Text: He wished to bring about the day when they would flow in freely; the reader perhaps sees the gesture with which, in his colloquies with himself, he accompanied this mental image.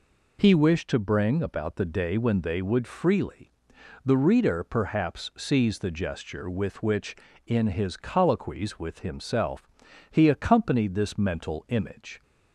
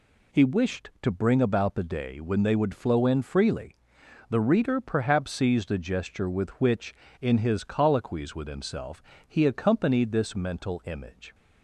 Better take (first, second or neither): second